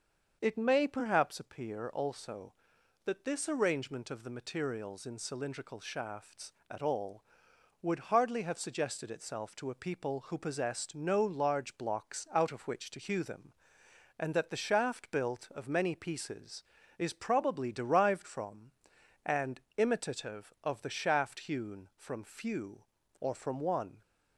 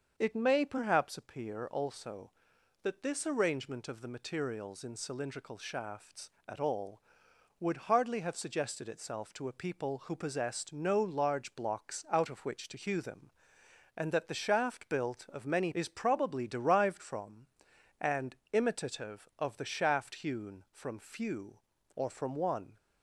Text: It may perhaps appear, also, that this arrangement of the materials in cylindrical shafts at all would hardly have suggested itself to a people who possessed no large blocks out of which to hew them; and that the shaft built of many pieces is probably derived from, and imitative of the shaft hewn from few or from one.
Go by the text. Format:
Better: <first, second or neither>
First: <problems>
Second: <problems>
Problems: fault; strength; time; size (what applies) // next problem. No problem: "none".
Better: first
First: starts louder than the rest; until 1.4 s; 6.5 dB // pauses between "and" and "imitative"; slight; at 19.6 s; 0.16 s long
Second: starts louder than the rest; until 1.1 s; 6.5 dB // skips "pieces"; at 15.7 s // pauses between "and" and "imitative"; slight; at 18.3 s; 0.16 s long